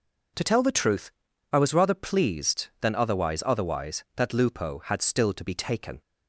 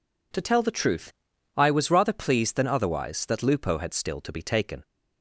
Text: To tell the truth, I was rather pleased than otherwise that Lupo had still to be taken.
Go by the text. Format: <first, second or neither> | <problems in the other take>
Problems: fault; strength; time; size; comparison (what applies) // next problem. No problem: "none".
second | says "otherwise" twice; at 3.4 s